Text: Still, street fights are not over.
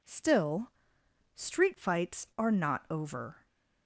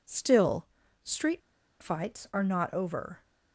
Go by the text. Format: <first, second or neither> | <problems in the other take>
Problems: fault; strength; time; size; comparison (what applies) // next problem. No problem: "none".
first | pauses between "street" and "fights"; at 1.4 s; 0.41 s long